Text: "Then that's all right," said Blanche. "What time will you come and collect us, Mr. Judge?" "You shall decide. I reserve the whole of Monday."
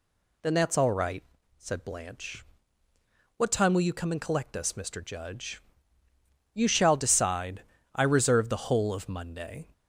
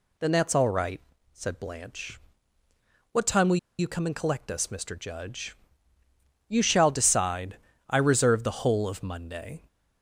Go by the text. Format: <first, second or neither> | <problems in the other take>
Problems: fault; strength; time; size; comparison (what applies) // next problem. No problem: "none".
first | pauses between "will" and "you"; slight; at 3.5 s; 0.21 s long